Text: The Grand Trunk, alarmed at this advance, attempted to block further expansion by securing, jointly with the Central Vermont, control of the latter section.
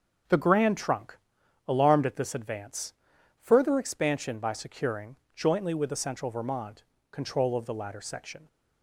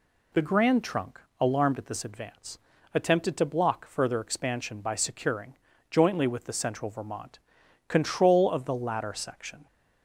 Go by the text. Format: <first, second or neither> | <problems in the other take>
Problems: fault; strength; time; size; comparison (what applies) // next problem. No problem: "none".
second | starts louder than the rest; until 1.7 s; 6.5 dB // skips "attempted to block"; at 3.1 s